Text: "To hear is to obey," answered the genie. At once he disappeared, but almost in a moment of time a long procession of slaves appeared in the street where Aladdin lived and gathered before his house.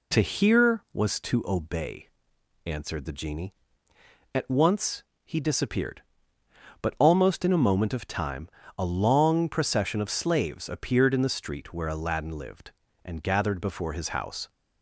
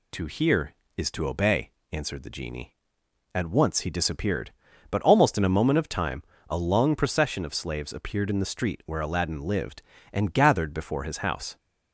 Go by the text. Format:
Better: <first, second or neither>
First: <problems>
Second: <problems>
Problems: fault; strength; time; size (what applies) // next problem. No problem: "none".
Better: second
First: says "was" for "is"; at 0.9 s // pauses between "once" and "he"; slight; at 5.0 s; 0.20 s long // pauses between "time" and "a"; slight; at 8.4 s; 0.28 s long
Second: pauses between "time" and "a"; slight; at 6.2 s; 0.26 s long